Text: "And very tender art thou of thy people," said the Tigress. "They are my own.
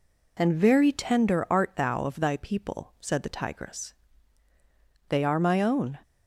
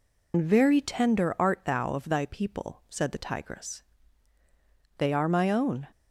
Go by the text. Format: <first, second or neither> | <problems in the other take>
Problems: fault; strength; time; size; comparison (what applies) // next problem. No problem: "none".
first | loses the start of "And"; at 0.3 s; 85 ms